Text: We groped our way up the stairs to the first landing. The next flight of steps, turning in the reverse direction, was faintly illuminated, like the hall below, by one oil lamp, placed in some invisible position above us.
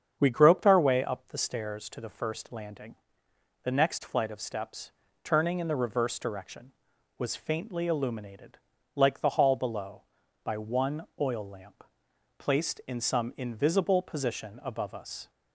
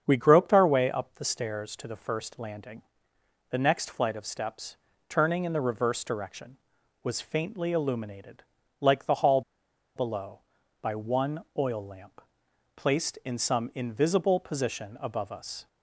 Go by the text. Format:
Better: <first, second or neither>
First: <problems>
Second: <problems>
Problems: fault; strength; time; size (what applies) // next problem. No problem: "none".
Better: first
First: starts louder than the rest; strong; until 1.2 s; 7.5 dB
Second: starts louder than the rest; strong; until 1.0 s; 7.5 dB // pauses between "hall" and "below"; noticeable; at 9.4 s; 0.55 s long